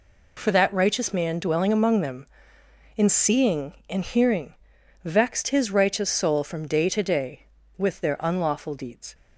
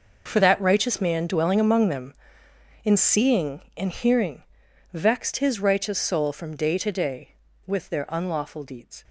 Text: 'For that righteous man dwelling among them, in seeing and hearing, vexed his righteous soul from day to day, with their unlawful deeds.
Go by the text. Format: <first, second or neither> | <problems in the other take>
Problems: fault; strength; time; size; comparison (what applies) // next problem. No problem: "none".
first | gets quieter; strong; throughout; 14.5 dB